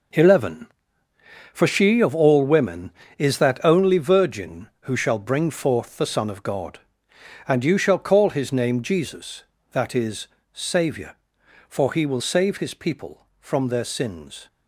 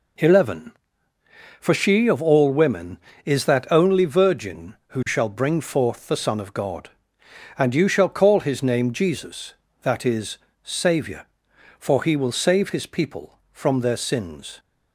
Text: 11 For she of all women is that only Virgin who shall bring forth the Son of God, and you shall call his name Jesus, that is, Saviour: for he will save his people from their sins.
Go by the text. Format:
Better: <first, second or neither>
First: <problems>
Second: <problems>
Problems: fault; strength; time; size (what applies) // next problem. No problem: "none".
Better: second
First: gets quieter; strong; throughout; 10.5 dB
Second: none